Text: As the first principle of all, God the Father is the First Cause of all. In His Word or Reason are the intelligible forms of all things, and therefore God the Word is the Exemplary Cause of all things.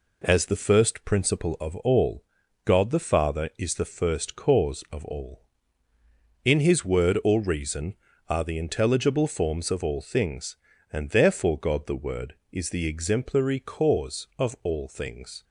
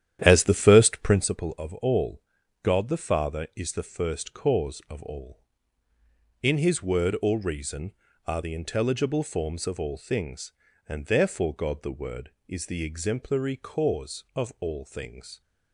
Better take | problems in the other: first | starts louder than the rest; strong; until 1.3 s; 10.5 dB

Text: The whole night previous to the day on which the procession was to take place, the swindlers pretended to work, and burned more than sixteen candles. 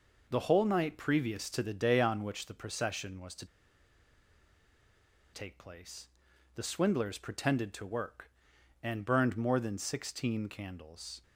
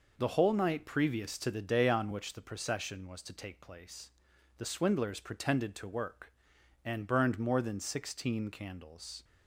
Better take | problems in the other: second | pauses between "to" and "take"; strong; at 3.4 s; 1.8 s long

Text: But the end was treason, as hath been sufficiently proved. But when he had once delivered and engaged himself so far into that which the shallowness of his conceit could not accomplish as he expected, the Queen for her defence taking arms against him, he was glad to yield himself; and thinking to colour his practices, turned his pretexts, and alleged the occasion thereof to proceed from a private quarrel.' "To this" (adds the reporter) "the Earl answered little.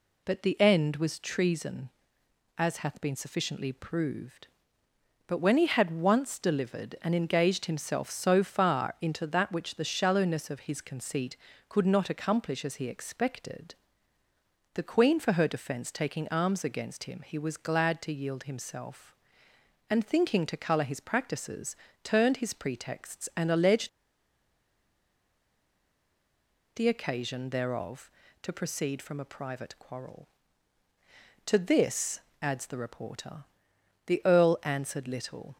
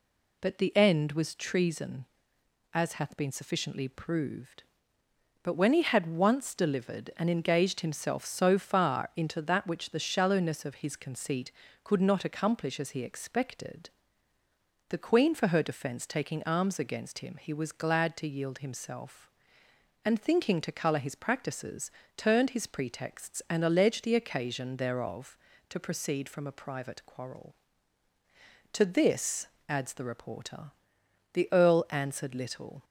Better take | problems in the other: second | pauses between "alleged" and "the"; strong; at 23.8 s; 2.8 s long

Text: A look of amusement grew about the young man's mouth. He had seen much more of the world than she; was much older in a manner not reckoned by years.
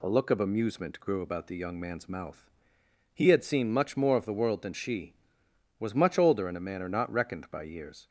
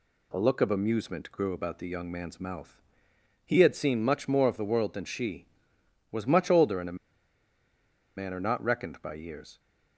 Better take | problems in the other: first | pauses between "a" and "manner"; at 6.9 s; 1.1 s long

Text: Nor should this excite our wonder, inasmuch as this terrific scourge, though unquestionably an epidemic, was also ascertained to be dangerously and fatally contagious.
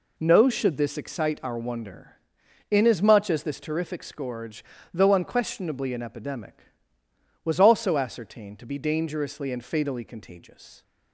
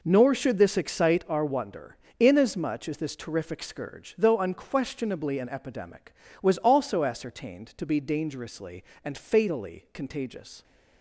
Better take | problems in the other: second | says "No" for "Nor"; at 0.1 s

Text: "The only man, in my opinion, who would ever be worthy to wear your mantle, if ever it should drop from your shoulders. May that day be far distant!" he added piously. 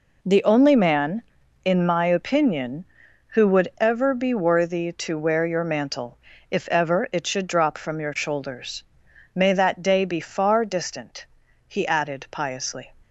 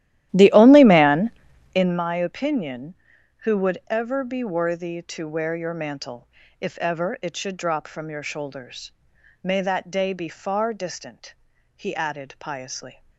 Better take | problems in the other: first | starts louder than the rest; strong; until 2.0 s; 13.5 dB

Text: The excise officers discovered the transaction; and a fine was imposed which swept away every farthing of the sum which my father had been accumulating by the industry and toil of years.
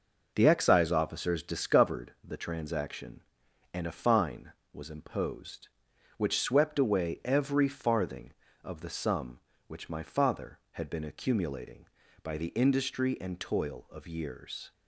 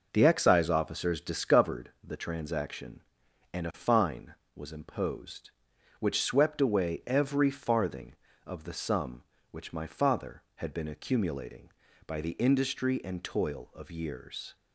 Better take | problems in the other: neither | none

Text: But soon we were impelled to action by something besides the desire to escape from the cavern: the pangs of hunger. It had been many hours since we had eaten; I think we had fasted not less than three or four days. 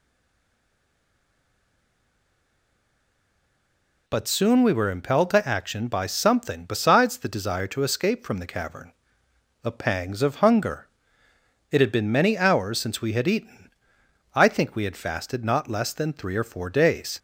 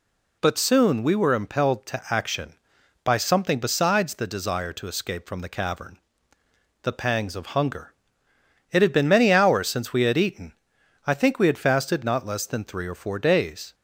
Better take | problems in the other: second | stays silent before the first word; strong; until 4.0 s; 4.0 s long

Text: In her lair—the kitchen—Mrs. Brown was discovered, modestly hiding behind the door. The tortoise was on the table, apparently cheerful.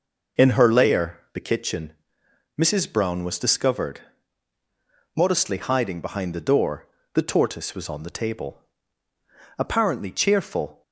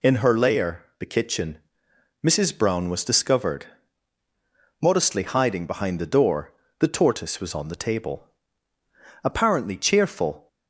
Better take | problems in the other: second | starts louder than the rest; noticeable; until 1.6 s; 5.5 dB

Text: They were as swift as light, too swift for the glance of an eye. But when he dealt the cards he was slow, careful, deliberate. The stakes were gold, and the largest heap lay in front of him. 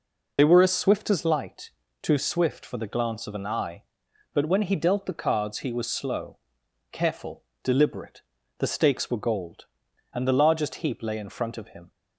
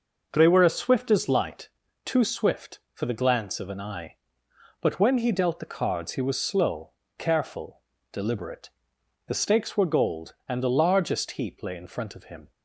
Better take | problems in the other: second | loses the start of "They"; at 0.3 s; 45 ms

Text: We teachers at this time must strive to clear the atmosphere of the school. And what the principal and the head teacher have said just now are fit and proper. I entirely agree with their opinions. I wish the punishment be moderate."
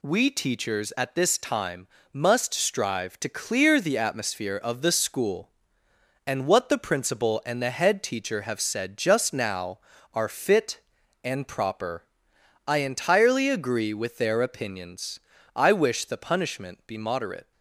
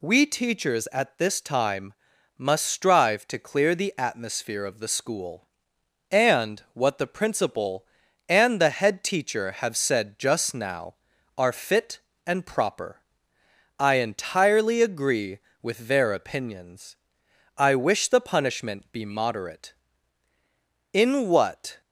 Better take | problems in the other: first | pauses between "time" and "must"; noticeable; at 1.9 s; 0.46 s long; slight in the first // goes on to say "In what"; noticeable; from 20.9 s on; 0.86 s long

